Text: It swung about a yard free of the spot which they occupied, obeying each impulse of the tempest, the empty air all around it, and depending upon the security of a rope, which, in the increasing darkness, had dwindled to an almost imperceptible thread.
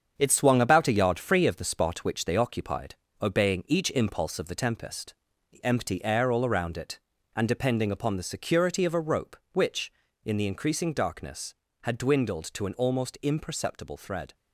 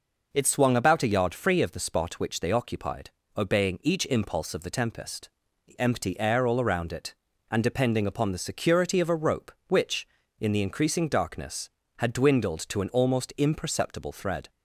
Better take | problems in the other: second | gets quieter; throughout; 6.5 dB

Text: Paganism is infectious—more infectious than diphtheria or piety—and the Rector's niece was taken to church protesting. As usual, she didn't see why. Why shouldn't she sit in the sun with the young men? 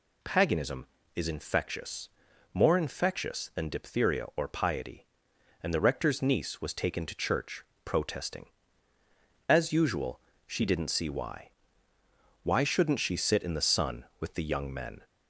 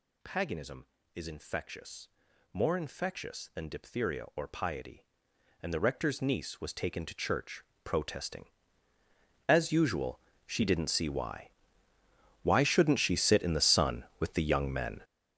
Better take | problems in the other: first | gets louder; strong; throughout; 12 dB // pauses between "church" and "protesting"; slight; at 7.6 s; 0.22 s long; slight in the first

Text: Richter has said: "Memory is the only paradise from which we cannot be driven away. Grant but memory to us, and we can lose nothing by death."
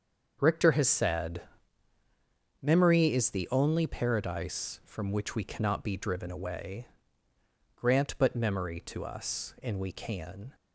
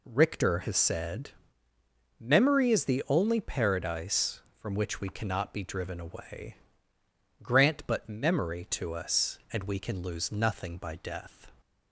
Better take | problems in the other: second | starts louder than the rest; until 1.4 s; 6.5 dB // stops before "lose nothing by death"; at 10.5 s

